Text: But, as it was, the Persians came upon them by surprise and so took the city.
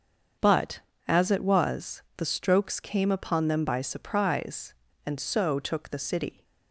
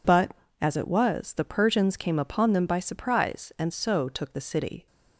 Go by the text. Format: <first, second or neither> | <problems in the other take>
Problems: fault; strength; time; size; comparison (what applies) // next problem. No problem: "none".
second | starts louder than the rest; until 1.6 s; 7 dB // says "Strokes" for "Persians"; at 2.2 s